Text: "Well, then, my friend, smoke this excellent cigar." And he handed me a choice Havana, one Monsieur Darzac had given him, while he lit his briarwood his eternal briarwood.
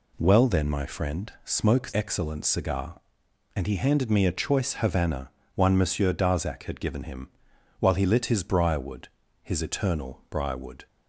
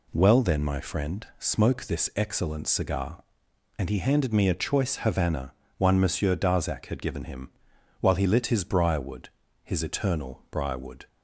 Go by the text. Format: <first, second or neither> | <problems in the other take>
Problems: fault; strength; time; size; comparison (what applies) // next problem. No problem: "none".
second | skips "this"; at 1.9 s // pauses between "briarwood" and "his"; slight; at 9.0 s; 0.36 s long; slight in the second